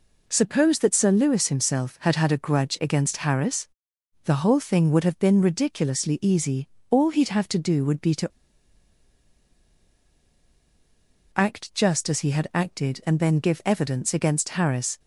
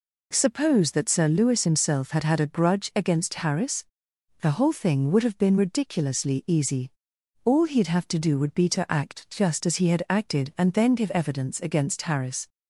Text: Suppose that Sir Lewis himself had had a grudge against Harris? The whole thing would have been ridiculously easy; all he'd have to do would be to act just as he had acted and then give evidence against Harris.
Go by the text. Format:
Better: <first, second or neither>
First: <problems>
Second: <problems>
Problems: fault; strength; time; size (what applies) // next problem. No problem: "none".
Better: second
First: pauses between "to" and "act"; strong; at 8.2 s; 3.0 s long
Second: none